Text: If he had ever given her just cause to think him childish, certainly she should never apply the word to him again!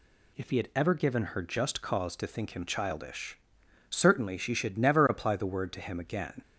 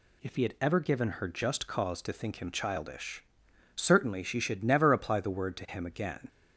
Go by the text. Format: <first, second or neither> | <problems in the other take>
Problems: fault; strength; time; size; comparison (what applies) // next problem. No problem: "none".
neither | none